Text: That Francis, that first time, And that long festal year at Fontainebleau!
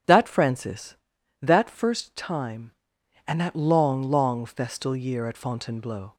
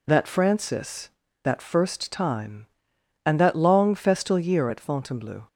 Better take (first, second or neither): second